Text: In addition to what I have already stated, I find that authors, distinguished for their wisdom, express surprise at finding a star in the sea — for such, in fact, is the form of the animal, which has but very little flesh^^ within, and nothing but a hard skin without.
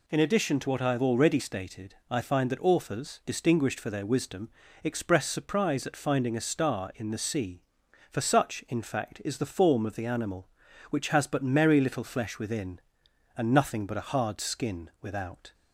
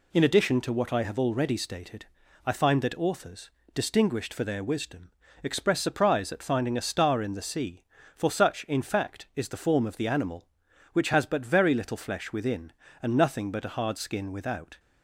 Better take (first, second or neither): second